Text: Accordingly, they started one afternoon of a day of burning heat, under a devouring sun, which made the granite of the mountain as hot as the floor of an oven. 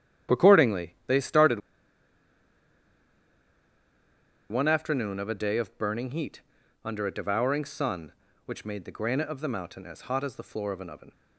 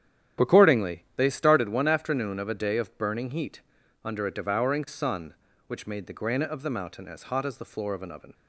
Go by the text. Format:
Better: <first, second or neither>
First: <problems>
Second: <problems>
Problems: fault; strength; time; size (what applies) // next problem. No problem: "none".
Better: second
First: starts louder than the rest; strong; until 1.4 s; 10.5 dB // pauses between "started" and "one"; strong; at 1.5 s; 2.9 s long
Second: starts louder than the rest; strong; until 1.5 s; 10.5 dB